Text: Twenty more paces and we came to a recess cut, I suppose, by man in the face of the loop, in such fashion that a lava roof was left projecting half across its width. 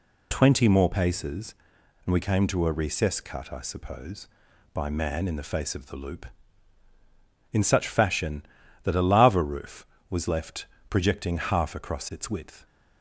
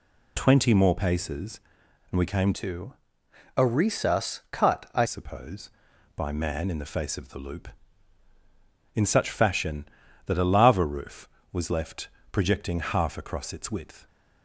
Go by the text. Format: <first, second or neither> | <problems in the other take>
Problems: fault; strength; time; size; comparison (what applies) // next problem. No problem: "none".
first | changes voice from "to" to "I"; from 2.5 to 5.0 s; 2.5 s long // pauses between "to" and "a"; noticeable; at 2.9 s; 0.62 s long // pauses between "left" and "projecting"; slight; at 12.0 s; 0.22 s long; slight in the first